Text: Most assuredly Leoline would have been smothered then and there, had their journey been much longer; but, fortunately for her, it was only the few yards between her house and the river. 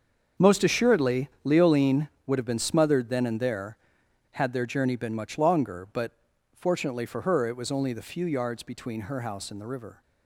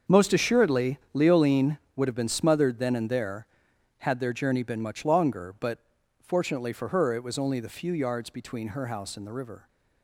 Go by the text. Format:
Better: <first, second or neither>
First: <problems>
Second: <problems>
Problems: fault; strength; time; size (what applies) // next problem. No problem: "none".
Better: neither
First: starts louder than the rest; until 1.5 s; 6.5 dB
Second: starts louder than the rest; until 1.2 s; 6.5 dB